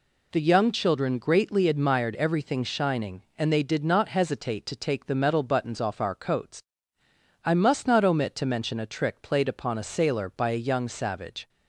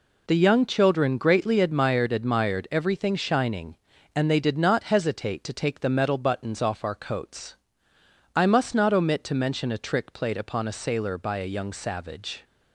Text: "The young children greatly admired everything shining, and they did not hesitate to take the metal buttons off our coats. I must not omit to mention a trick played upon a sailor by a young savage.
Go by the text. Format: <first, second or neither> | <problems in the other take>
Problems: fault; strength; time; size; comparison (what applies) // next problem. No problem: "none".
first | says "admired" twice; at 2.1 s